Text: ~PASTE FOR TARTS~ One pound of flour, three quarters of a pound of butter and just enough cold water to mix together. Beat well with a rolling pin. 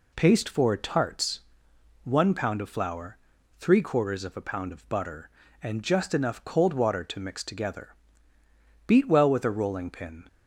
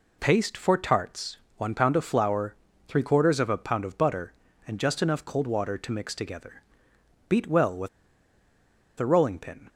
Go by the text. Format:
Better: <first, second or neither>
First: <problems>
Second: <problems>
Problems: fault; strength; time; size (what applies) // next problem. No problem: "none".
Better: first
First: none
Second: pauses between "with" and "a"; at 7.8 s; 1.0 s long